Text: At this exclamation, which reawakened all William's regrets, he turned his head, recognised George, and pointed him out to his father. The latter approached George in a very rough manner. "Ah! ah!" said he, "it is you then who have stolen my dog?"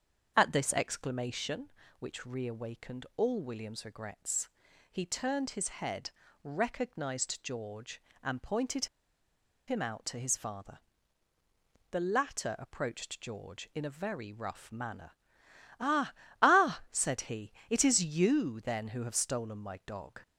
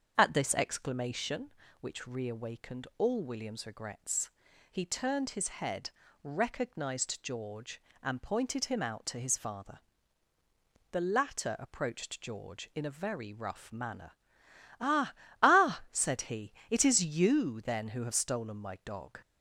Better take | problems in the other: second | starts louder than the rest; until 1.3 s; 7 dB; also in the second // pauses between "pointed" and "him"; noticeable; at 8.8 s; 0.81 s long

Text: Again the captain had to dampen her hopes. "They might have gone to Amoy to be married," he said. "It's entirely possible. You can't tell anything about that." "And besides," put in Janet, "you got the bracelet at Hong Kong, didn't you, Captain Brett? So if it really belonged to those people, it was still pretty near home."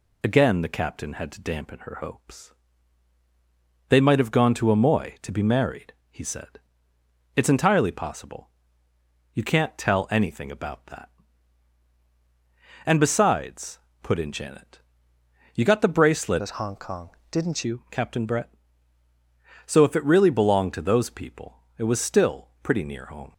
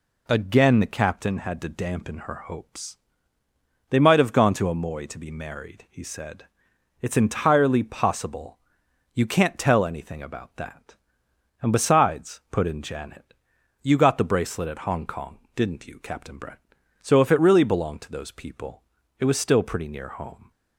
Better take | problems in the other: second | changes voice from "at" to "didn't"; from 16.4 to 17.6 s; 1.2 s long

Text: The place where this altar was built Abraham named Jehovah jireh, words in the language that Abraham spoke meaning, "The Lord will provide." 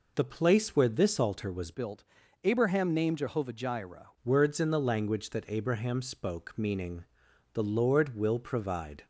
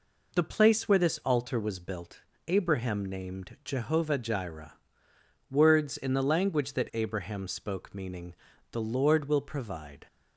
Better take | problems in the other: second | changes voice from "built" to "jireh"; from 1.7 to 4.0 s; 2.3 s long // pauses between "built" and "Abraham"; at 2.0 s; 0.42 s long; slight in the second

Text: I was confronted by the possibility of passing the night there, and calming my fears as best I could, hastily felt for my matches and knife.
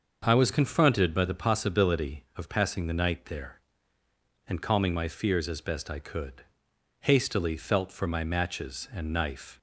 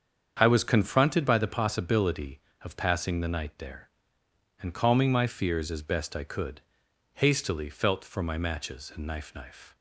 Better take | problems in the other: first | starts louder than the rest; strong; until 1.4 s; 7.5 dB; also in the first // says "knife" twice; at 9.3 s

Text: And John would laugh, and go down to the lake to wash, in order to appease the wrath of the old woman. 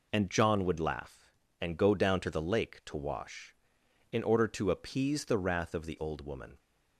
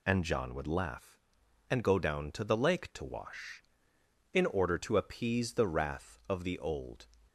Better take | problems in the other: first | stops before "woman"; at 7.2 s

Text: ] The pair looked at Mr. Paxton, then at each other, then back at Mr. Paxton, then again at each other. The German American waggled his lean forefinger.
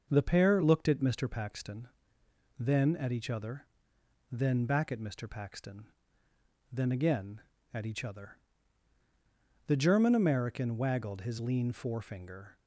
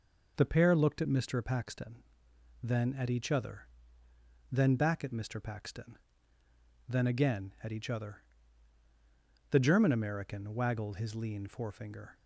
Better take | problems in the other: neither | none

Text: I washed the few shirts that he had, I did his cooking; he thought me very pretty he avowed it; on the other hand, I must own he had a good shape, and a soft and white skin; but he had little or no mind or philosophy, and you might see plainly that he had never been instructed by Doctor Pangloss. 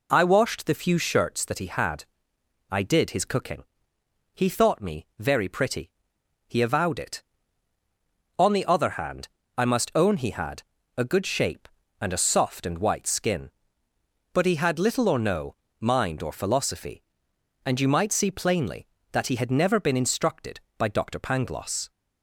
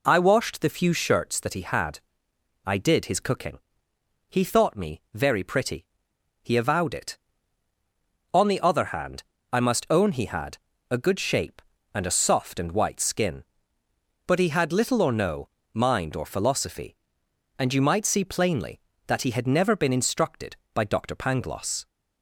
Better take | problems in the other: neither | pauses between "pretty" and "he"; noticeable; the same in both // pauses between "had" and "a"; slight; the same in both // pauses between "no" and "mind"; slight; the same in both

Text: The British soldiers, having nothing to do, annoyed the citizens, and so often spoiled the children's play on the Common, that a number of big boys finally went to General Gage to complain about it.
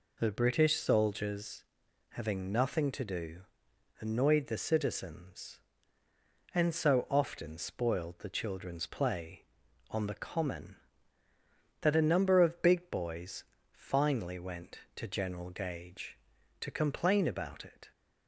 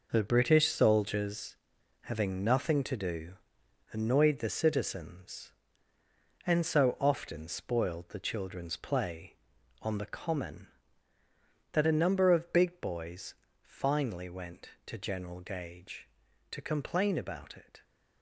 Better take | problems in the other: first | gets quieter; strong; throughout; 9 dB // pauses between "boys" and "finally"; slight; at 13.3 s; 0.30 s long; slight in the first

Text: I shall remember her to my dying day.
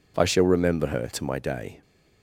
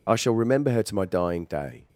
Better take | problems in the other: second | skips "dying"; at 1.3 s

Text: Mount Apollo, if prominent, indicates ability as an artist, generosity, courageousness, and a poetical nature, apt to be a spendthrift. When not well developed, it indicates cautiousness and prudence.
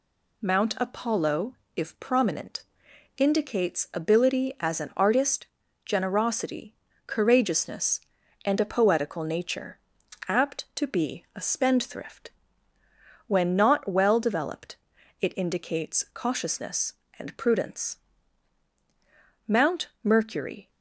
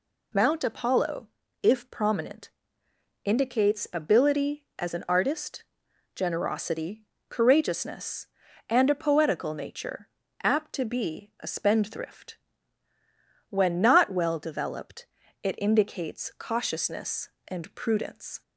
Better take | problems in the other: second | goes on to say "Mount Mercury"; noticeable; from 19.4 s on; 1.2 s long

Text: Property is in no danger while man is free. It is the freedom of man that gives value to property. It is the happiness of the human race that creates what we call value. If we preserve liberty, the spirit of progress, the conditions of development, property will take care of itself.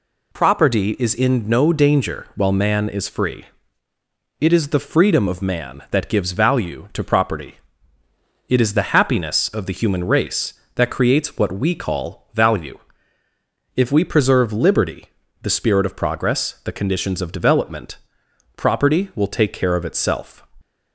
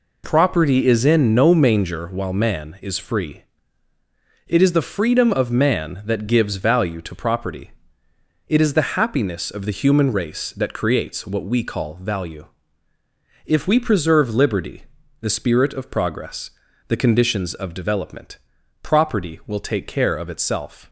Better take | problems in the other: first | says "manger" for "danger"; at 1.5 s

